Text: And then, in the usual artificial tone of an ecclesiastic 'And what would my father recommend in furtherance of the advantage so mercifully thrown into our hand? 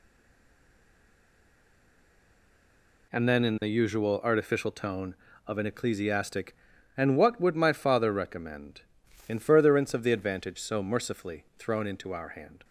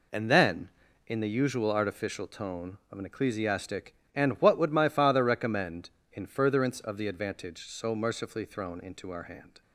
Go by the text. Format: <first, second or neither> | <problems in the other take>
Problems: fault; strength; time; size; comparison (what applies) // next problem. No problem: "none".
second | stays silent before the first word; strong; until 3.1 s; 3.1 s long